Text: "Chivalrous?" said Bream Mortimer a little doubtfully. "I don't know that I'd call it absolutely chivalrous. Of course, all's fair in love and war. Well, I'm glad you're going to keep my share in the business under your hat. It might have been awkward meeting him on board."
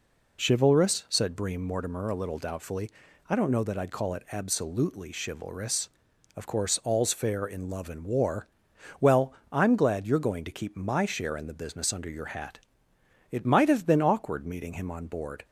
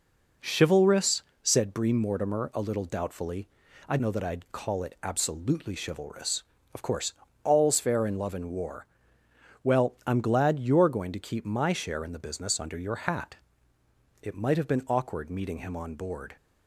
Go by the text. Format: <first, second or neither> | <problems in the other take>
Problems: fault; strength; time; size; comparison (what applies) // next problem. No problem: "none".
first | skips "don't"; at 3.9 s